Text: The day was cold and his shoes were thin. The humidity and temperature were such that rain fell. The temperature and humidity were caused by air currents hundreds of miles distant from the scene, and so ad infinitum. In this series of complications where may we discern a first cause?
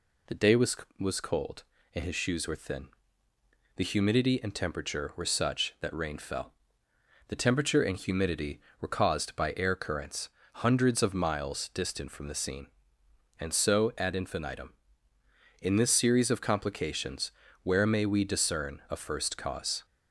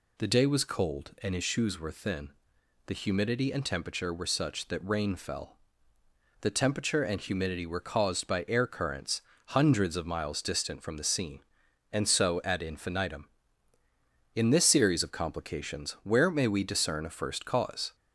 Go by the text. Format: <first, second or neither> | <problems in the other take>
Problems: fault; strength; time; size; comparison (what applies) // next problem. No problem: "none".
second | says "was" twice; at 0.9 s // pauses between "currents" and "hundreds"; slight; at 10.2 s; 0.36 s long; slight in the second // pauses between "complications" and "where"; slight; at 17.3 s; 0.32 s long